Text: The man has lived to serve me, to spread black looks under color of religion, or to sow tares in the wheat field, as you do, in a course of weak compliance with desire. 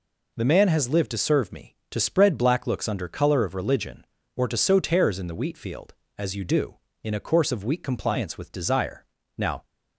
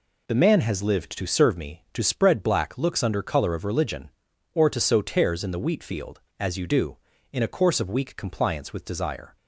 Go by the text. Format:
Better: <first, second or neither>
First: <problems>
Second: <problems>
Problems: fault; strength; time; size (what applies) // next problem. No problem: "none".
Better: second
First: goes on to say "Now"; slight; from 9.3 s on; 0.28 s long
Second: none